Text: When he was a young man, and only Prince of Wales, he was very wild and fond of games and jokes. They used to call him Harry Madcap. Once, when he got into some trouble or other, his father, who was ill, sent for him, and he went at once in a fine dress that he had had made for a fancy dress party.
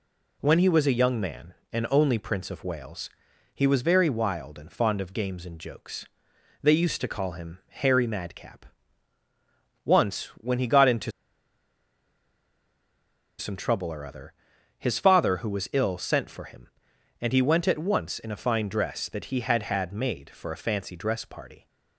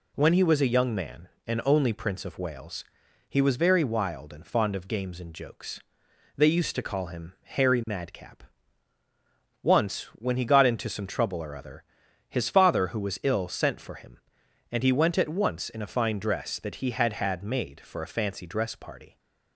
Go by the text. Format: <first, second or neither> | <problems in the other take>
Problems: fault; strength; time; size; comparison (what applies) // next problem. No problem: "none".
second | pauses between "into" and "some"; strong; at 11.1 s; 2.2 s long